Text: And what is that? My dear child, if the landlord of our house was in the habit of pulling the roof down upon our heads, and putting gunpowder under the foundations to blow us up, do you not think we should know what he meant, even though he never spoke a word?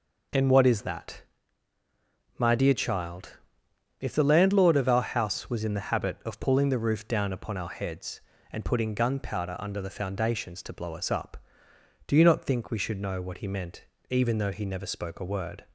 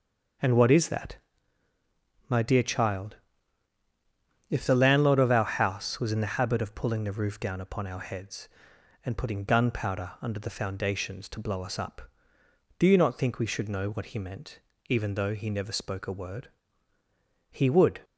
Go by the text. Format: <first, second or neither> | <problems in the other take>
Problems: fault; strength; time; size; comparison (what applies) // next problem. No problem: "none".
first | starts louder than the rest; noticeable; until 2.5 s; 6 dB // goes on to say "He would"; from 17.5 s on; 0.50 s long